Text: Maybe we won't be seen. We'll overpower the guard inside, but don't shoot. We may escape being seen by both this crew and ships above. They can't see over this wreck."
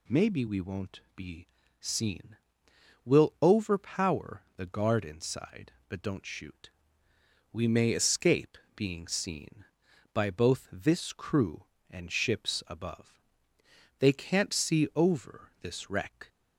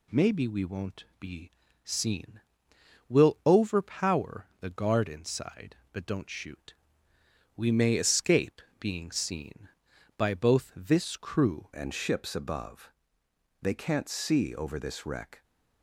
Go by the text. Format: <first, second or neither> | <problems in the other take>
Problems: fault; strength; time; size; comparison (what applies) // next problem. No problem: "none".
first | pauses between "won't" and "be"; slight; at 1.0 s; 0.16 s long; slight in the first // pauses between "be" and "seen"; slight; at 1.5 s; 0.34 s long; slight in the first // pauses between "escape" and "being"; slight; at 8.6 s; 0.18 s long; slight in the first // changes voice at "and"; from 11.7 s on; 3.7 s long